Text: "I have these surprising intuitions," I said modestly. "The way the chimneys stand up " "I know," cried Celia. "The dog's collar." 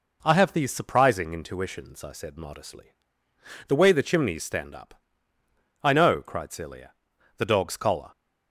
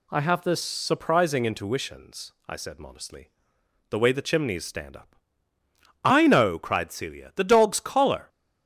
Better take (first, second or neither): first